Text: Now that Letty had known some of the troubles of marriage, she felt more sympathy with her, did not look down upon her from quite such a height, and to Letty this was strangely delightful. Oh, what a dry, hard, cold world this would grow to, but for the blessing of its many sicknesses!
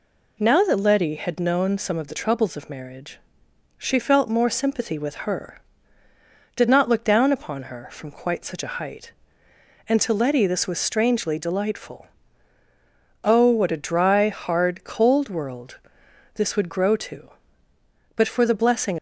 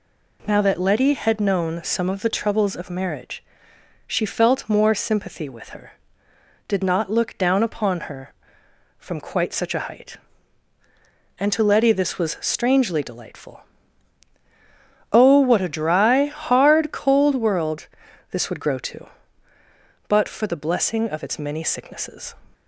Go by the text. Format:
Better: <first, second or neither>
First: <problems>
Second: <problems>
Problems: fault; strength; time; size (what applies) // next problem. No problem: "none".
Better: second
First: pauses between "world" and "this"; noticeable; at 15.7 s; 0.54 s long // stops before "of its many sicknesses"; at 18.9 s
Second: pauses between "world" and "this"; at 17.8 s; 0.44 s long